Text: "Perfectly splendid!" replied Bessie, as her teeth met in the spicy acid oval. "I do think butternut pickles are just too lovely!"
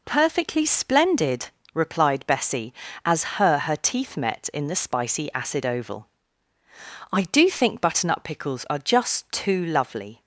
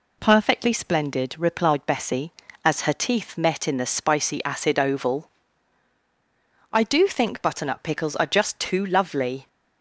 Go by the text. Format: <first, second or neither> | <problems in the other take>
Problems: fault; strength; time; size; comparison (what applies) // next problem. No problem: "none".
second | says "her" twice; at 3.5 s